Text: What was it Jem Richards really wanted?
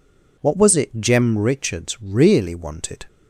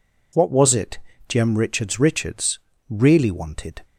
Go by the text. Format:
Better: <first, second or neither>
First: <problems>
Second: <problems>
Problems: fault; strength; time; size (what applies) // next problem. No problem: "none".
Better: first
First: none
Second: pauses between "it" and "Jem"; slight; at 0.9 s; 0.30 s long // says "Richards" twice; at 1.9 s